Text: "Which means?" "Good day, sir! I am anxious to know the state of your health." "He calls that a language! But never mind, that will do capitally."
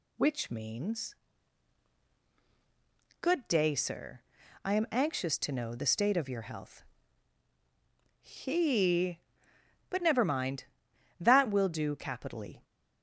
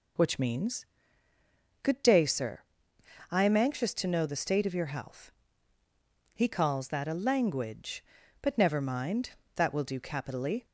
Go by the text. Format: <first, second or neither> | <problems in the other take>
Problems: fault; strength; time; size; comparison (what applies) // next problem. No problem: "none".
second | skips "calls that a language"; at 9.5 s